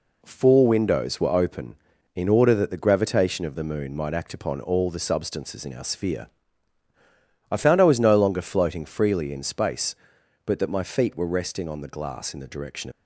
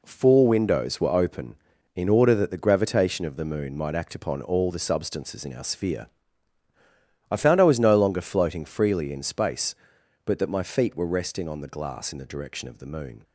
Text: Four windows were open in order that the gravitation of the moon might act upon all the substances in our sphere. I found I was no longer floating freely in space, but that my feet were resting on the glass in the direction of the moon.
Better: second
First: stops before "of the moon"; at 12.9 s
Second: none

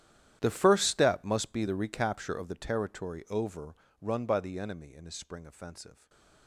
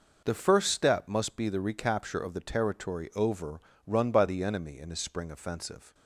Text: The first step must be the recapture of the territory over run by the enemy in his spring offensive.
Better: second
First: gets quieter; strong; throughout; 20 dB // pauses between "over" and "run"; slight; at 3.7 s; 0.28 s long // stays silent after the last word; slight; from 5.9 s on; 0.5 s long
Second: pauses between "over" and "run"; slight; at 3.5 s; 0.28 s long

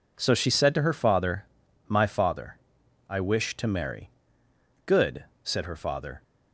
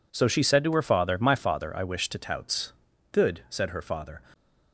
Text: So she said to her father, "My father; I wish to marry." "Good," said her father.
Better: first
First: none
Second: says "touts" for "marry"; at 2.1 s

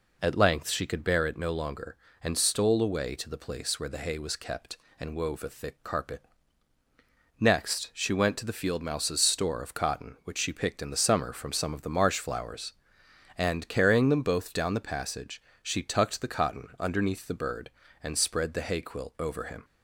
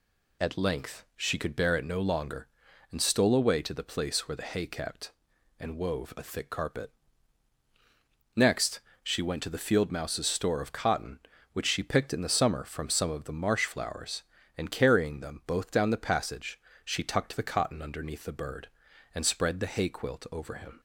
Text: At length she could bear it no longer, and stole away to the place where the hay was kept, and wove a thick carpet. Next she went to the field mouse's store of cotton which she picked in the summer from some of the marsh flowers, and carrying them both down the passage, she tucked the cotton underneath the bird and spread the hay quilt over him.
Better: first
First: none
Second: skips "was"; at 4.6 s // pauses between "Next" and "she"; slight; at 8.7 s; 0.22 s long

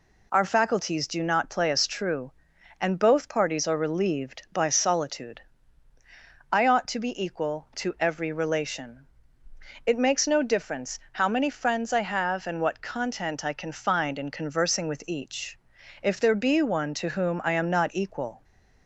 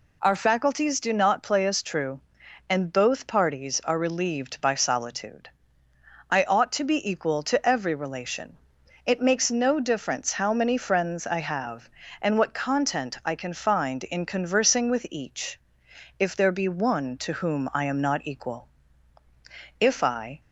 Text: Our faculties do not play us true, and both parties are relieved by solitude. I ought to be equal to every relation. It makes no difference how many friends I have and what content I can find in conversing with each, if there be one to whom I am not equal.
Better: first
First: none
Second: goes on to say "If I"; noticeable; from 19.7 s on; 0.62 s long

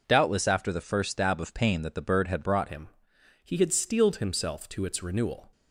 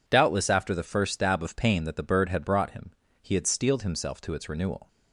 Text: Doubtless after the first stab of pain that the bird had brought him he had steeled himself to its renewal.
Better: second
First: changes voice at "him"; from 2.6 s on; 2.9 s long // pauses between "him" and "he"; noticeable; at 2.8 s; 0.54 s long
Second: pauses between "him" and "he"; slight; at 2.9 s; 0.30 s long

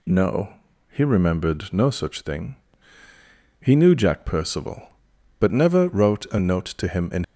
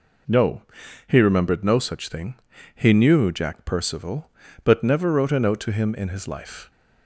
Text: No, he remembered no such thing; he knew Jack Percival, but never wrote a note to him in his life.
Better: second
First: stops before "his life"; at 7.2 s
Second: none

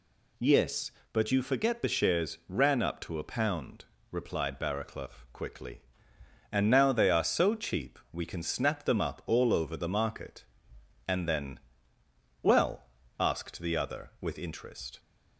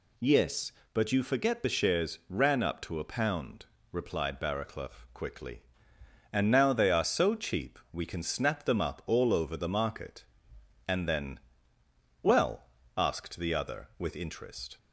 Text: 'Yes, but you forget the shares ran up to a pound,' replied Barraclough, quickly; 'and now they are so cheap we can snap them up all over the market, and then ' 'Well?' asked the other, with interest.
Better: neither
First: none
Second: none

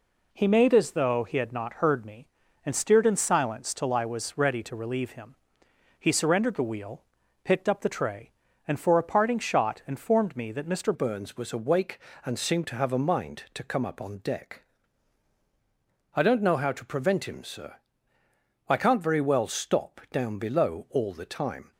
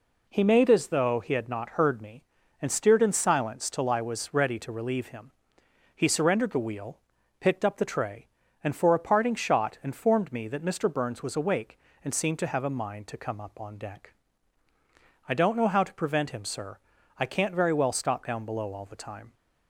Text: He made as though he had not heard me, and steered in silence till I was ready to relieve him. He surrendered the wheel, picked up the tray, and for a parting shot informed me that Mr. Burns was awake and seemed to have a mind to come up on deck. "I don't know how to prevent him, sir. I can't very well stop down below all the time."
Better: second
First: changes voice at "Burns"; from 10.9 s on; 10.8 s long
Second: none

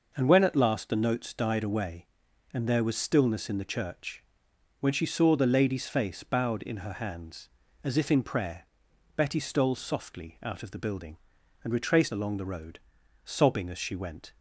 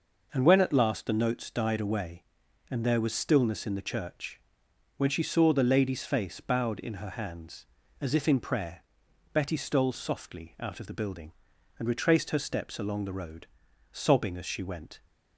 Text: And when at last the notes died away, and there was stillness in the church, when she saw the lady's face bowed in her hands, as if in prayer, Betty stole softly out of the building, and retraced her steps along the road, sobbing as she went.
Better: second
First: skips "her steps"; at 12.1 s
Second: none

